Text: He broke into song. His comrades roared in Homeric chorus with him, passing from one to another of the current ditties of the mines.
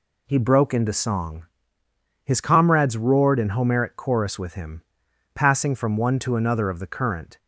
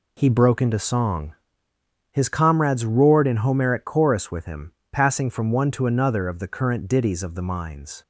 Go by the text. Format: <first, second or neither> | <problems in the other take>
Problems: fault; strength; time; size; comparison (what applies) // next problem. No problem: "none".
second | stops before "ditties of the mines"; at 7.3 s